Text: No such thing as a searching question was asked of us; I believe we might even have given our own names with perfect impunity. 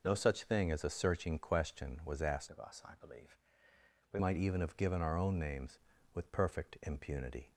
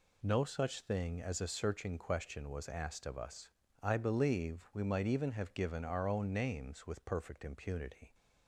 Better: second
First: changes voice from "of" to "we"; from 2.5 to 4.1 s; 1.6 s long // pauses between "believe" and "we"; noticeable; at 3.3 s; 0.76 s long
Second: none

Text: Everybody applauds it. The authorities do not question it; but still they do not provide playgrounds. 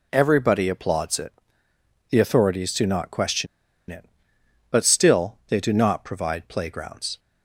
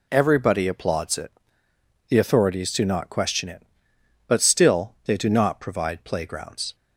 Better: second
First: pauses between "question" and "it"; at 3.4 s; 0.44 s long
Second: none

